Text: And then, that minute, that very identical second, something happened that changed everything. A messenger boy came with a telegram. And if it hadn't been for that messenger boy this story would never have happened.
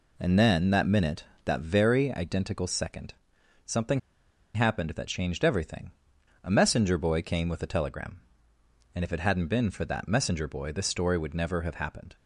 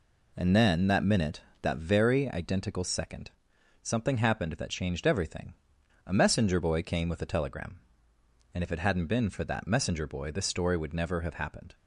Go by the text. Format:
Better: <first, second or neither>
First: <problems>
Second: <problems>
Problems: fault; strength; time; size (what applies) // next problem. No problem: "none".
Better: second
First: pauses between "something" and "happened"; noticeable; at 3.9 s; 0.55 s long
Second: none